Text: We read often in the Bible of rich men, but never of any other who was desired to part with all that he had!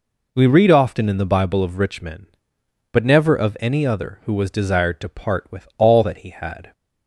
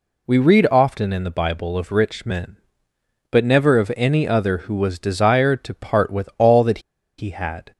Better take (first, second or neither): first